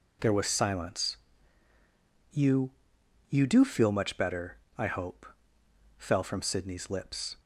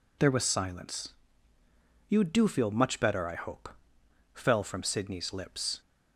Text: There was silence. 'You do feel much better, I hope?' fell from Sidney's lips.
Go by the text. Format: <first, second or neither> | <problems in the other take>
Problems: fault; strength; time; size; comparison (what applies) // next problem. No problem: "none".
second | says "You" twice; at 3.3 s